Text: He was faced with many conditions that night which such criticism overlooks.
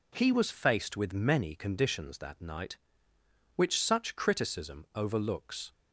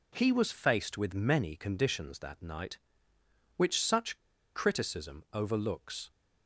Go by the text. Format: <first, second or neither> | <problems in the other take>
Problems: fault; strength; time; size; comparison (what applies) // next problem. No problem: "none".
first | pauses between "such" and "criticism"; at 4.1 s; 0.39 s long